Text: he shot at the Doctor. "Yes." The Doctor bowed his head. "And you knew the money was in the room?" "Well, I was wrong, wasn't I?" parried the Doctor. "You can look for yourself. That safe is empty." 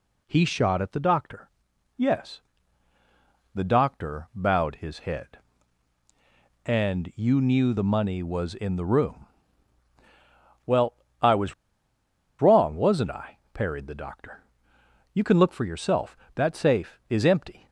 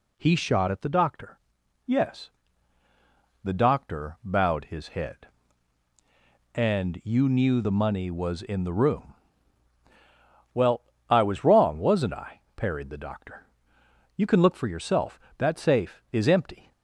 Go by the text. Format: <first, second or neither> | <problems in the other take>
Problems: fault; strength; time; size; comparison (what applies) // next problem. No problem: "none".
second | pauses between "was" and "wrong"; noticeable; at 11.5 s; 0.87 s long